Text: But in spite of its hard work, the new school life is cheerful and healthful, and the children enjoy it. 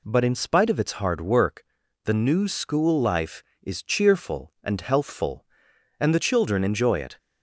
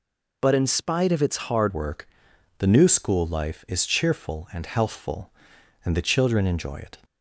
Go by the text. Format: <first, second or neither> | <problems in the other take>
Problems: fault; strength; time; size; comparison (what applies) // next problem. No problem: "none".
first | changes voice at "work"; from 1.7 s on; 5.2 s long